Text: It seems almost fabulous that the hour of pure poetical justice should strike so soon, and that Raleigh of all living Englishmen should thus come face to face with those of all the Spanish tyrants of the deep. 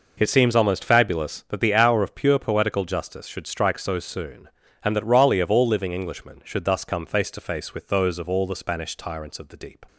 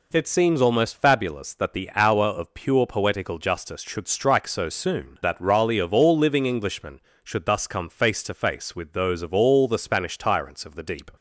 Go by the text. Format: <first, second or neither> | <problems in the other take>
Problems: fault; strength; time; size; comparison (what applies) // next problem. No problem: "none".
first | skips "and"; at 5.2 s